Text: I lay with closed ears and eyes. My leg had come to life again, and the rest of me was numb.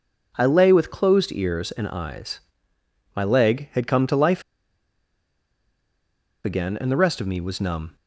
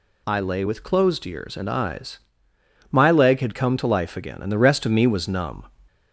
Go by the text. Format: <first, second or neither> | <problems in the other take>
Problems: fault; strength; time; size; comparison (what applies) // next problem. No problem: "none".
second | pauses between "life" and "again"; strong; at 4.4 s; 2.0 s long